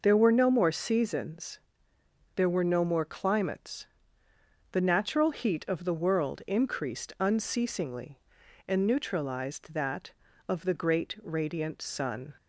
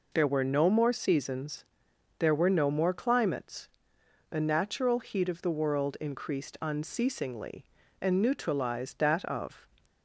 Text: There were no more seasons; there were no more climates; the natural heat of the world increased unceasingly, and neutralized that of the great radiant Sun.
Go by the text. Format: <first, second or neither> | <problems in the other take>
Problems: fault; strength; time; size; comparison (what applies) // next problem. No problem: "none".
first | stops before "the great radiant Sun"; at 9.8 s